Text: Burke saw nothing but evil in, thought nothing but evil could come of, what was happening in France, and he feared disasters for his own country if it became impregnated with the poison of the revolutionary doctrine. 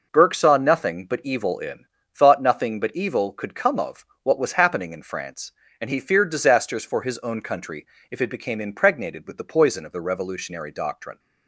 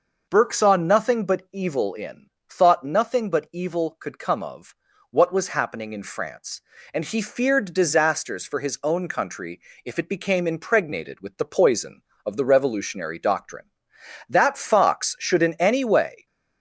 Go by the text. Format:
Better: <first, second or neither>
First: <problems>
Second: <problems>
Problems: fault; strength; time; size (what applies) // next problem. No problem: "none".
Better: first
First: pauses between "country" and "if"; slight; at 7.8 s; 0.24 s long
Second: pauses between "country" and "if"; slight; at 9.6 s; 0.24 s long // goes on to say "That Fox should in any way"; strong; from 14.2 s on; 1.9 s long